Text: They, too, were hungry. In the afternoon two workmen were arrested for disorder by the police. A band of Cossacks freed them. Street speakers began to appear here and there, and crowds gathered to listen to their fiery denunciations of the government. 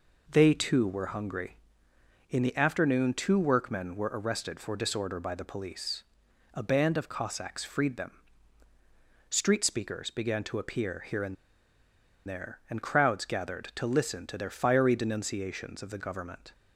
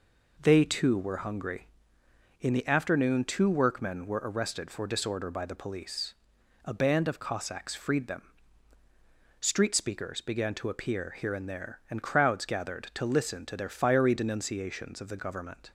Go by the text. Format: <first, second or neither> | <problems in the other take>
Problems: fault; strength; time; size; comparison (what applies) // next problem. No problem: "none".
second | pauses between "and" and "there"; noticeable; at 11.3 s; 0.93 s long